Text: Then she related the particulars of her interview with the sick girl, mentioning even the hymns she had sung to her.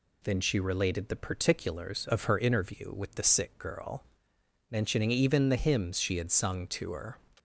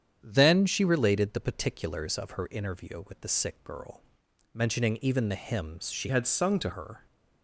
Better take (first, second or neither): first